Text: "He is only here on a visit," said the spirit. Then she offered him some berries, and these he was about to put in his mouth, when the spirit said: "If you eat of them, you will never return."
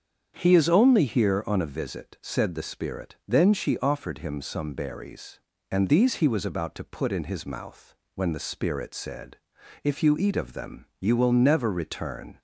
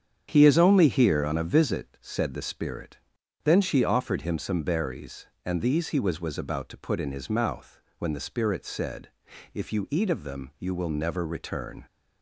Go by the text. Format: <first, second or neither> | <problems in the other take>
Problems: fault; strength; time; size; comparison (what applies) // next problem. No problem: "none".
first | starts louder than the rest; strong; until 1.3 s; 8 dB; strong in the first // says "was" twice; at 6.2 s